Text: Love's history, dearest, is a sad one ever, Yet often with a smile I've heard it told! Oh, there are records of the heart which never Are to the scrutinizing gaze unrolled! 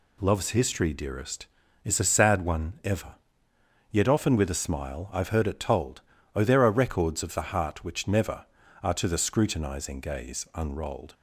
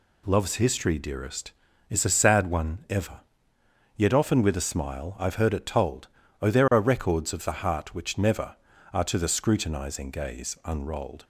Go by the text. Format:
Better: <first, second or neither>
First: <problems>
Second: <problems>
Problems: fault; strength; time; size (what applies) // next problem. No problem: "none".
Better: neither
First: none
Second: none